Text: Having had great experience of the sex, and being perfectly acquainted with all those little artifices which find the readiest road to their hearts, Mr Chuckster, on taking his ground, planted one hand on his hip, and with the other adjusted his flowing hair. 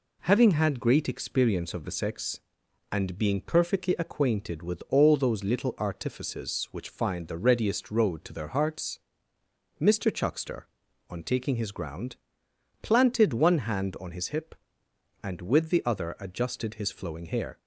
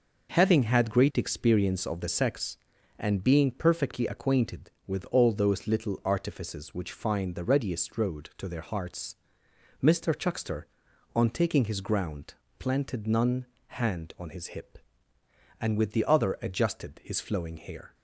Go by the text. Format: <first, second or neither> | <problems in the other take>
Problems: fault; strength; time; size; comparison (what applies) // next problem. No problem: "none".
first | says "none" for "one"; at 13.0 s